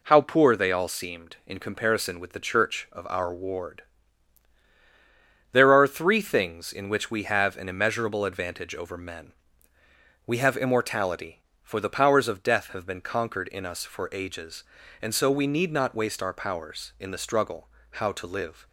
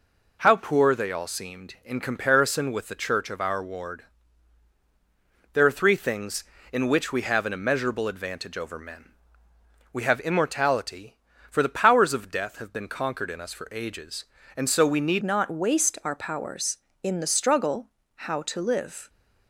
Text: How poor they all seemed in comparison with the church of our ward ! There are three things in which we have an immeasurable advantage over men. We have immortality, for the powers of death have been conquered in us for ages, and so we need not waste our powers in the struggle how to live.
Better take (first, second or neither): first